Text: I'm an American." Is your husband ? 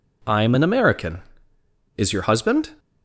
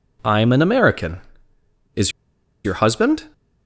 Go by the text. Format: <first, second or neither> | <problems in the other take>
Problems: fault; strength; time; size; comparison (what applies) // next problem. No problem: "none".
first | pauses between "Is" and "your"; noticeable; at 2.1 s; 0.54 s long